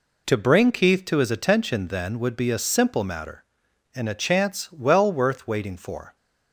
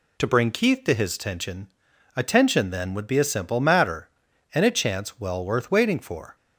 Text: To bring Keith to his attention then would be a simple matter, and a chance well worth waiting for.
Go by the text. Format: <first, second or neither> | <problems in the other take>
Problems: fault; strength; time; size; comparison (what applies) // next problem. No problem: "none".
first | says "attention" twice; at 2.1 s